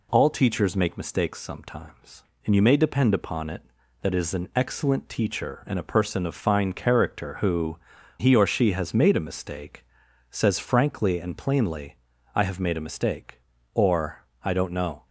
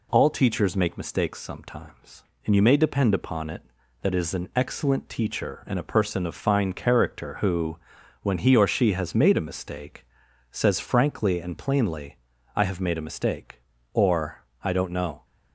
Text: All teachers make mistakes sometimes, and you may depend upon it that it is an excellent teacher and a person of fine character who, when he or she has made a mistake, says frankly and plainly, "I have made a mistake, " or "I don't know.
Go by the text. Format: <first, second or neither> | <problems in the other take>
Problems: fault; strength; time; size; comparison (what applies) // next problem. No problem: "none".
second | skips "when"; at 7.9 s // pauses between "or" and "I"; slight; at 14.2 s; 0.16 s long; slight in the second